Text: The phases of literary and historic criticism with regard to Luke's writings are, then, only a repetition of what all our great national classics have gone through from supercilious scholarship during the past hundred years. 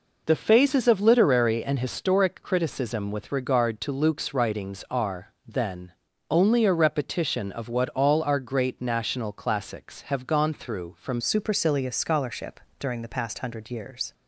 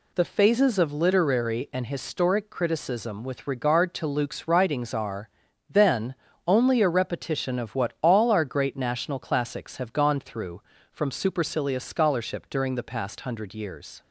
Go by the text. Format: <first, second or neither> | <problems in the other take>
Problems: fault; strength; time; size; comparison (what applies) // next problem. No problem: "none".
second | changes voice at "supercilious"; from 11.1 s on; 3.0 s long // pauses between "scholarship" and "during"; slight; at 12.5 s; 0.20 s long